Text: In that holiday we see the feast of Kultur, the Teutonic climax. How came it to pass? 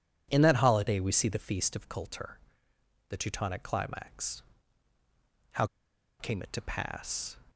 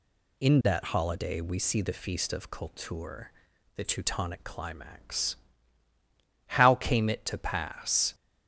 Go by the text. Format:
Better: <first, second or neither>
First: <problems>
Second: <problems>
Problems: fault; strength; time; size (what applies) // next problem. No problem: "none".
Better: second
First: pauses between "How" and "came"; noticeable; at 5.6 s; 0.54 s long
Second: none